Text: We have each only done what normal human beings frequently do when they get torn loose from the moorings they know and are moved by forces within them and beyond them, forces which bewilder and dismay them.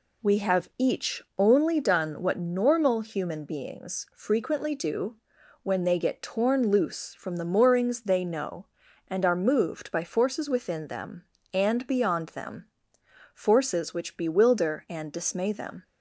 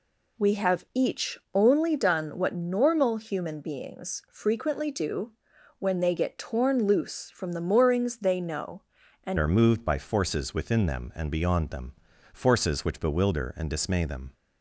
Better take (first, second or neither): first